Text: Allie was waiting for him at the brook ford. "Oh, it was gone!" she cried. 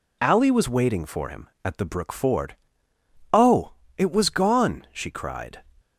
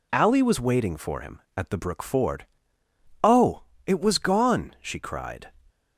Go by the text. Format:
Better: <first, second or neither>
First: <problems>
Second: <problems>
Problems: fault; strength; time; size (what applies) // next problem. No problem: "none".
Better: neither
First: none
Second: none